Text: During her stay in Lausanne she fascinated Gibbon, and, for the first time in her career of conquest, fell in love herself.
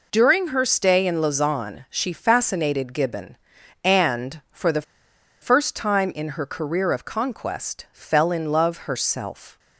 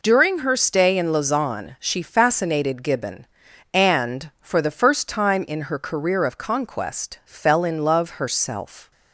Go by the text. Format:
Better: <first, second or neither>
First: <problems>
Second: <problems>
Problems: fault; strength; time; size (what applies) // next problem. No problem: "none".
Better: second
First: pauses between "the" and "first"; noticeable; at 4.8 s; 0.59 s long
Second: none